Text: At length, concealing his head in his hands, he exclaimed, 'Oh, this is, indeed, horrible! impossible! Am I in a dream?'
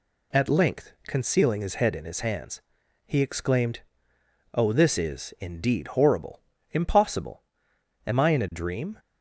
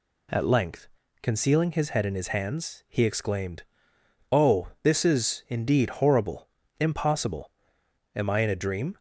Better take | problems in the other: neither | none

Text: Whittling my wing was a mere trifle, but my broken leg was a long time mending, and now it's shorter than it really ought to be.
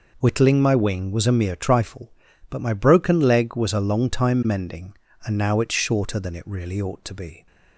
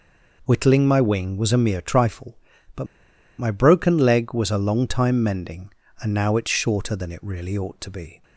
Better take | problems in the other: first | pauses between "but" and "my"; noticeable; at 2.8 s; 0.52 s long

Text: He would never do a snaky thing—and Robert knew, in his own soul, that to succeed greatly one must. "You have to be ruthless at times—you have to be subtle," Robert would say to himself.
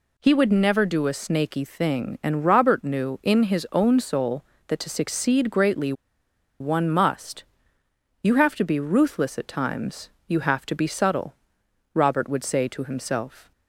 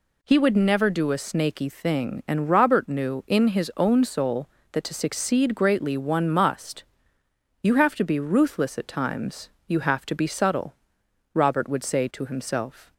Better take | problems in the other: second | pauses between "greatly" and "one"; noticeable; at 5.9 s; 0.67 s long

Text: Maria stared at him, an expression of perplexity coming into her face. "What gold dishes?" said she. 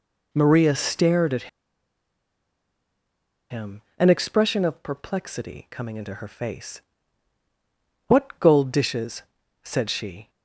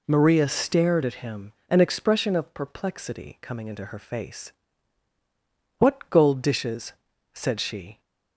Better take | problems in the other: second | pauses between "at" and "him"; strong; at 1.4 s; 2.0 s long

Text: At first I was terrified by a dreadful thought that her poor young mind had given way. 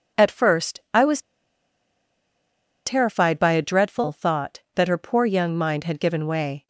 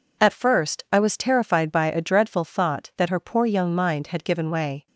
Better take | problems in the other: second | pauses between "was" and "terrified"; strong; at 1.2 s; 1.6 s long

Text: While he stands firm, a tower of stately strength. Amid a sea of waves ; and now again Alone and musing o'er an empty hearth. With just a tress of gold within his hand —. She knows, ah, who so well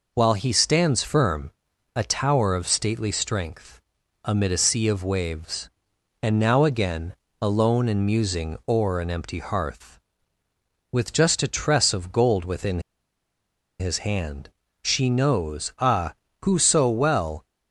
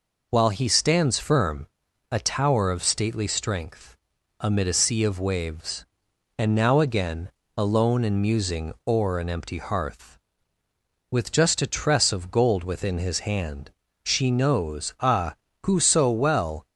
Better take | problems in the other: second | pauses between "again" and "Alone"; slight; at 7.1 s; 0.26 s long; slight in the second // pauses between "within" and "his"; at 12.8 s; 0.99 s long

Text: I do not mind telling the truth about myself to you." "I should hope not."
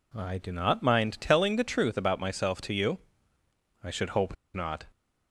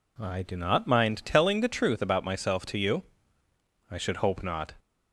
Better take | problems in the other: second | pauses between "hope" and "not"; slight; at 4.3 s; 0.20 s long

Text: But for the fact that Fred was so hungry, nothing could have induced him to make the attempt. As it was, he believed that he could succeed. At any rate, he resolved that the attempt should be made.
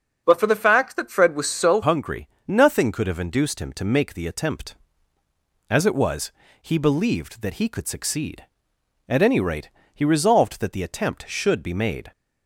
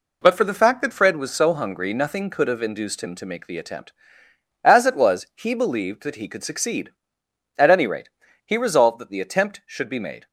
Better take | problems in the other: second | starts louder than the rest; until 1.2 s; 7 dB // changes voice at "hungry"; from 1.8 s on; 10.3 s long

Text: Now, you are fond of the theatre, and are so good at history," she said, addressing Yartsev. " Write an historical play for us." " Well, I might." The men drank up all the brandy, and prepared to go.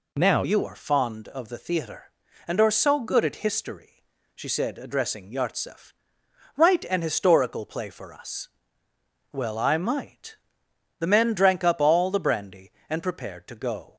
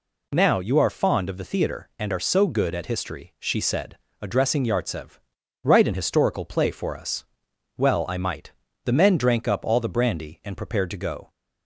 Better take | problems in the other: second | changes voice at "you"; from 0.4 s on; 13.5 s long

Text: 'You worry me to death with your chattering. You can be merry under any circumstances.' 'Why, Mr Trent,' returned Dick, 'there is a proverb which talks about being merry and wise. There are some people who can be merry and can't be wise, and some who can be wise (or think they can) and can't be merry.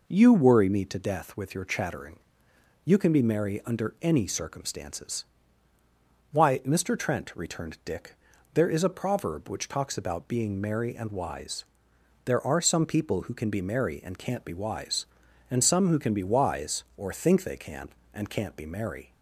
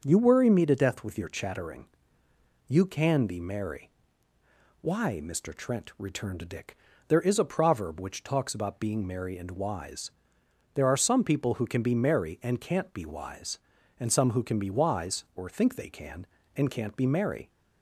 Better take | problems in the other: first | starts louder than the rest; until 1.0 s; 6.5 dB // skips "under any circumstances"; at 4.3 s

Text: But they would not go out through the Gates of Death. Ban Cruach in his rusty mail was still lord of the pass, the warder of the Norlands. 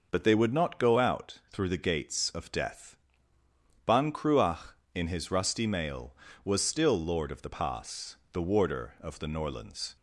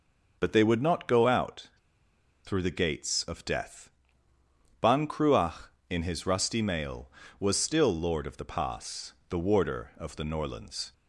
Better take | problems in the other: first | pauses between "out" and "through"; noticeable; at 1.6 s; 0.76 s long

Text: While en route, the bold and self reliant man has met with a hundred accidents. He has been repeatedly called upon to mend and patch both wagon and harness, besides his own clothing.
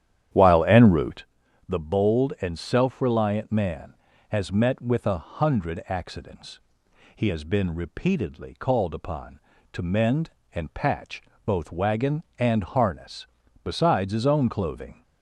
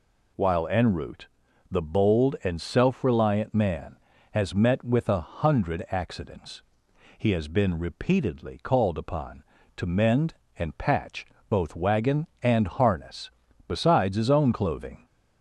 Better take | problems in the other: second | starts louder than the rest; strong; until 1.2 s; 10.5 dB // pauses between "patch" and "both"; slight; at 11.2 s; 0.24 s long; slight in the second

